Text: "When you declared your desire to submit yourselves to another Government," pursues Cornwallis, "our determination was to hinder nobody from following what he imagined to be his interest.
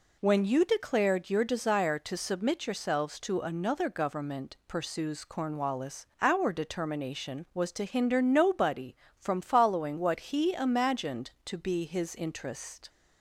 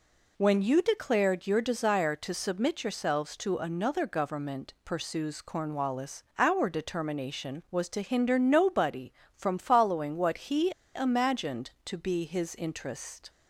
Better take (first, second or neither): first